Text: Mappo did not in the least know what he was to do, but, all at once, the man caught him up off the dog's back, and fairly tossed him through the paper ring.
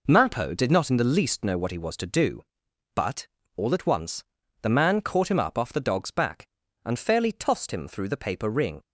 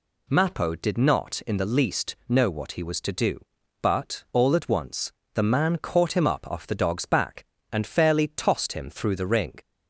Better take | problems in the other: first | skips "paper"; at 9.2 s

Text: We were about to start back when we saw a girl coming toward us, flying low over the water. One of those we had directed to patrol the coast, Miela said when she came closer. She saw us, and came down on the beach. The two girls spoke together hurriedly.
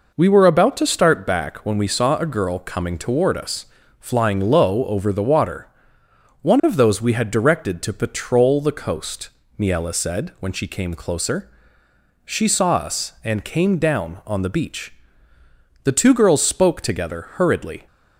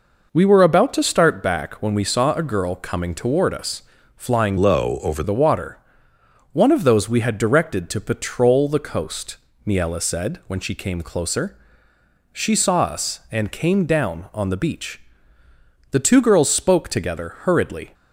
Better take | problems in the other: first | changes voice from "low" to "over"; from 4.5 to 5.2 s; 0.7 s long

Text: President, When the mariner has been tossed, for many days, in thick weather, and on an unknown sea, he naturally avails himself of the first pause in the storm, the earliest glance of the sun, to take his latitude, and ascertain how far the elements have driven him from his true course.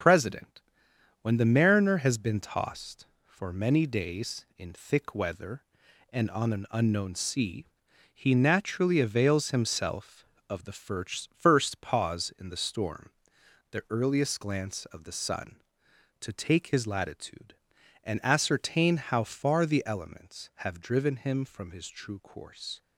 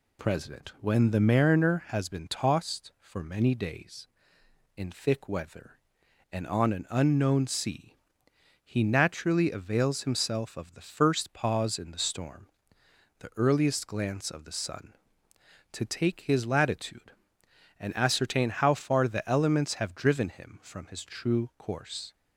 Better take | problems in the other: second | says "first" twice; at 11.3 s

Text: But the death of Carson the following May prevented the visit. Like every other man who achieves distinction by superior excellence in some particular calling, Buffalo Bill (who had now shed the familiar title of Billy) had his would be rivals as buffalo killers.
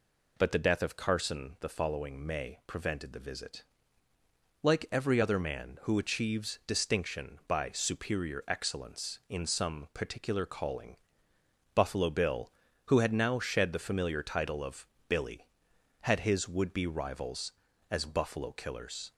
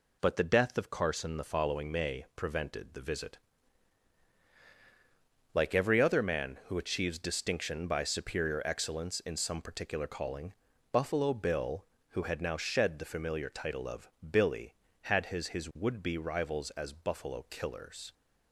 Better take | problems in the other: first | pauses between "of" and "Billy"; slight; at 14.0 s; 0.20 s long; slight in the first // says "his" twice; at 15.5 s

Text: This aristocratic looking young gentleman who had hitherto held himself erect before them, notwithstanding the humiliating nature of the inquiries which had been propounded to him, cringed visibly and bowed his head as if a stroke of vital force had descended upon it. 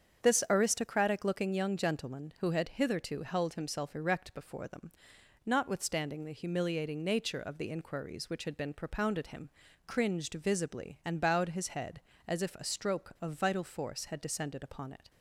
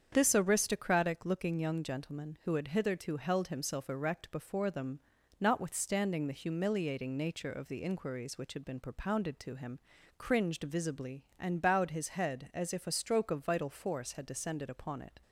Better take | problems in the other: second | starts louder than the rest; strong; until 1.2 s; 7.5 dB; strong in the second // skips "to"; at 9.2 s

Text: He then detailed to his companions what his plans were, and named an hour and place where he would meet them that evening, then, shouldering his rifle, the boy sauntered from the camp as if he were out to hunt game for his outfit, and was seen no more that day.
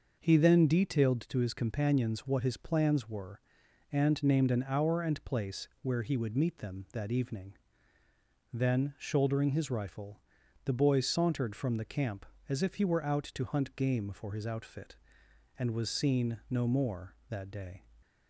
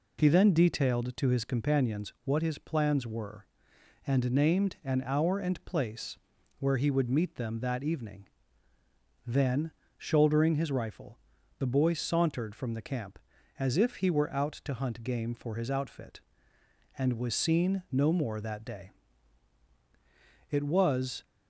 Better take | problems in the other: first | pauses between "place" and "where"; at 6.1 s; 0.40 s long // goes on to say "It was"; noticeable; from 20.4 s on; 0.74 s long

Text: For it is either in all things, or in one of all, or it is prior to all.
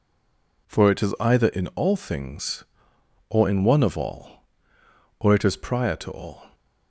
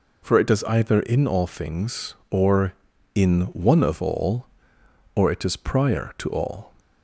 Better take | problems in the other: second | stays silent before the first word; slight; until 0.6 s; 0.6 s long

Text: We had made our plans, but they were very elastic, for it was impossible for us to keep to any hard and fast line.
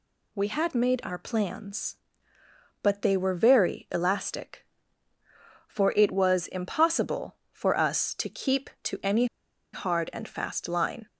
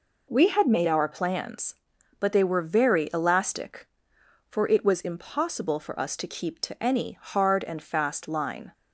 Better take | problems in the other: second | pauses between "any" and "hard"; noticeable; at 9.2 s; 0.48 s long

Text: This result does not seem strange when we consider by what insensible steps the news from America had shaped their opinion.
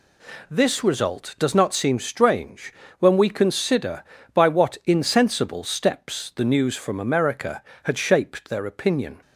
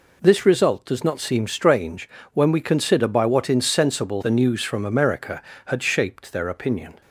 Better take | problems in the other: first | pauses between "strange" and "when"; slight; at 2.0 s; 0.24 s long; slight in the first // skips "steps"; at 4.2 s

